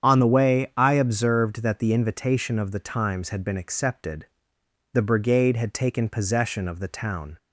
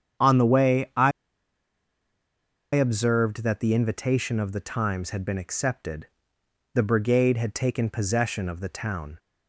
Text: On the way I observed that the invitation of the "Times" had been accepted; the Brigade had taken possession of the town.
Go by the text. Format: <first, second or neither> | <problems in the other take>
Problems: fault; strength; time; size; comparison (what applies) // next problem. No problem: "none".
first | starts louder than the rest; strong; until 2.8 s; 8.5 dB; strong in the first // pauses between "I" and "observed"; strong; at 1.1 s; 1.6 s long